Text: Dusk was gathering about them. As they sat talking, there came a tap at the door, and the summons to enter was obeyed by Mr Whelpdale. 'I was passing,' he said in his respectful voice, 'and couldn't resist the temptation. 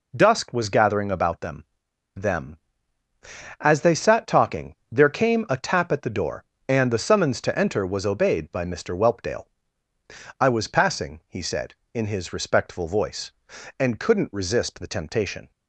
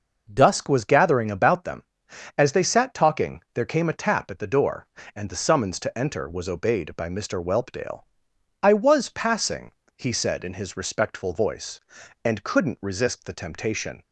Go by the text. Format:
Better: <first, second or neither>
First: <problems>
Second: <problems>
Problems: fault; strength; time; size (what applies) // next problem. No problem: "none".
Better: second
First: says "them" twice; at 2.1 s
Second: none